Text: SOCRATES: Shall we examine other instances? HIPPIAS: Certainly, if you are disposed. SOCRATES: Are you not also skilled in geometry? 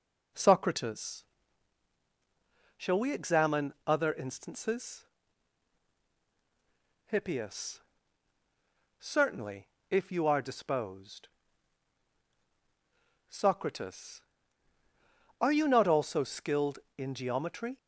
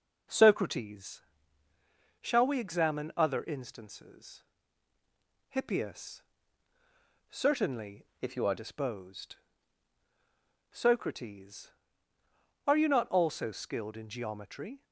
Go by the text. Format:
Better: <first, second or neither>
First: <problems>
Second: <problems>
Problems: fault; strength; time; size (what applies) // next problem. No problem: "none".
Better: first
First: none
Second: changes voice from "if" to "are"; from 8.2 to 8.5 s; 0.3 s long